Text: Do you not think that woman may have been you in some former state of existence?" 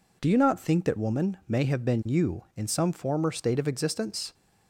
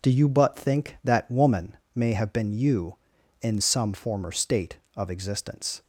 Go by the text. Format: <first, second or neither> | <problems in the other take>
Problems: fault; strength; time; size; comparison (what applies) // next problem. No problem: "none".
first | says "but" for "not"; at 0.2 s // pauses between "woman" and "may"; slight; at 1.7 s; 0.18 s long